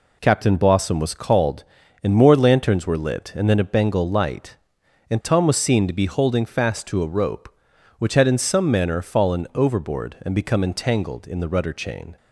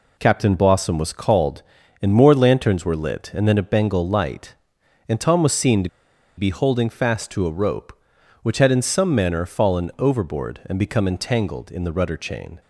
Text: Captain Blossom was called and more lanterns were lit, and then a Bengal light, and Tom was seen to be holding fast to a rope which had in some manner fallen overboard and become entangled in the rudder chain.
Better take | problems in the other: first | pauses between "to" and "be"; noticeable; at 5.8 s; 0.49 s long

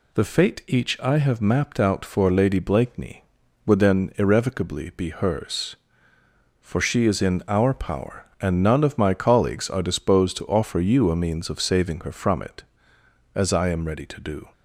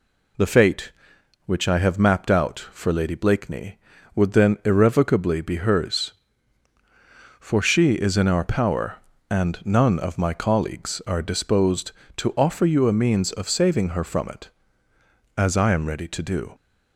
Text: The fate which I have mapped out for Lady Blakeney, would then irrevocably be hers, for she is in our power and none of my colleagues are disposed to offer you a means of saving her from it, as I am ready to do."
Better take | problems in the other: second | says "each" for "which"; at 0.6 s

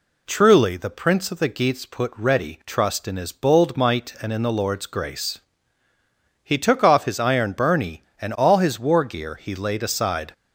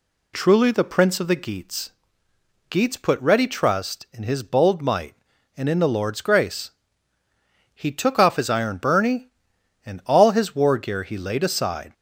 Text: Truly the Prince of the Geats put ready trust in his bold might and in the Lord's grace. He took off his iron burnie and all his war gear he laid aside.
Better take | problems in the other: first | says "Geats" twice; at 2.6 s

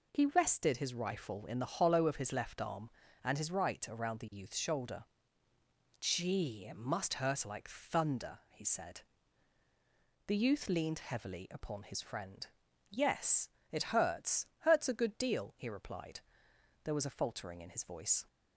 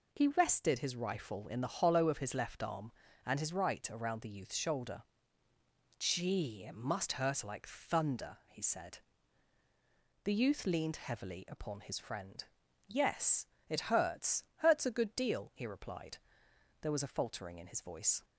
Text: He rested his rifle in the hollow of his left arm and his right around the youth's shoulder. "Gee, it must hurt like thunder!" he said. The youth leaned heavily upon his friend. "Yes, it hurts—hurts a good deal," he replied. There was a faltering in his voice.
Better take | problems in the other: neither | none

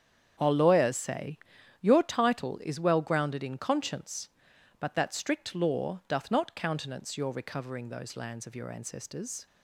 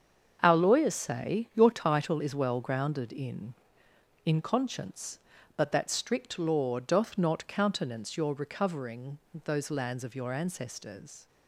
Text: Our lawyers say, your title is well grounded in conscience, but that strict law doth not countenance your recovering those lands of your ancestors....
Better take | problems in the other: first | starts louder than the rest; until 1.4 s; 7 dB; strong in the first // says "in" twice; at 4.2 s // pauses between "recovering" and "those"; slight; at 9.1 s; 0.28 s long

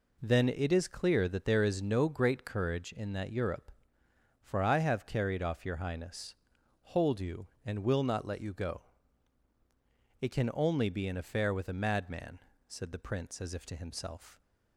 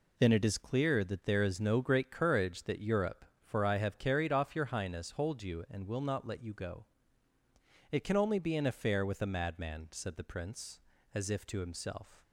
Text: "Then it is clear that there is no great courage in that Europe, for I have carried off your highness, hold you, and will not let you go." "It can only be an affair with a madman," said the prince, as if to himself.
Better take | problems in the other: first | skips "in"; at 2.6 s

